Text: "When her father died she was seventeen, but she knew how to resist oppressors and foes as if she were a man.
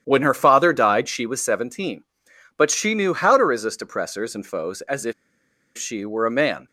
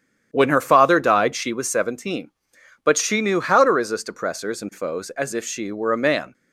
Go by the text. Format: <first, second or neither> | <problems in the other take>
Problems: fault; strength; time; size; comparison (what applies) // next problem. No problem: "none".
second | starts louder than the rest; strong; until 1.0 s; 10 dB; strong in the second // pauses between "if" and "she"; noticeable; at 5.1 s; 0.65 s long